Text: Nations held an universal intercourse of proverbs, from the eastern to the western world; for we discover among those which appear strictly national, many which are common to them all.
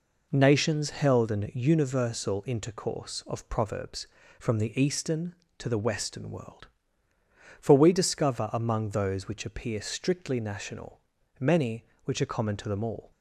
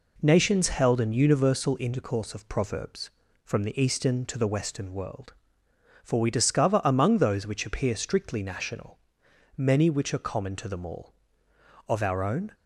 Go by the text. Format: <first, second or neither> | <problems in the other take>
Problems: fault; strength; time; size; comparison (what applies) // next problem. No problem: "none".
first | goes on to say "Of our own"; noticeable; from 11.8 s on; 0.66 s long